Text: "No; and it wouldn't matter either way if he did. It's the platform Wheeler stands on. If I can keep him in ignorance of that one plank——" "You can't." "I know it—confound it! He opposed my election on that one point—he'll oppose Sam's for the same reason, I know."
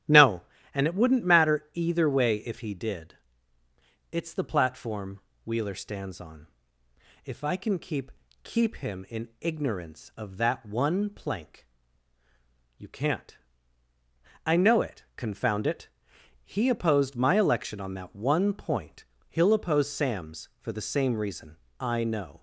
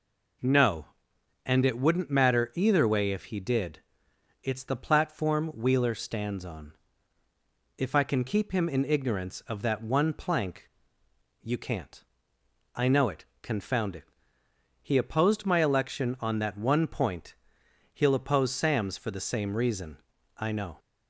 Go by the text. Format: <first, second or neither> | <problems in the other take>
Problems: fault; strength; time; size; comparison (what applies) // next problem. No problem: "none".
second | starts louder than the rest; strong; until 1.4 s; 11.5 dB // pauses between "platform" and "Wheeler"; slight; at 5.2 s; 0.24 s long // says "keep" twice; at 8.4 s